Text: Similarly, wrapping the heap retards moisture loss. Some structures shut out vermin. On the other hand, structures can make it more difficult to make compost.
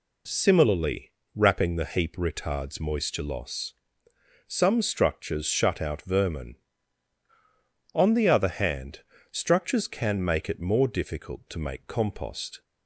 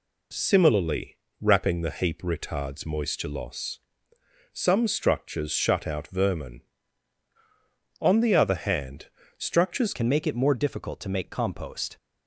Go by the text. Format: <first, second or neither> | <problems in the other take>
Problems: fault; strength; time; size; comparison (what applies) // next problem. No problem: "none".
first | changes voice at "can"; from 9.9 s on; 2.0 s long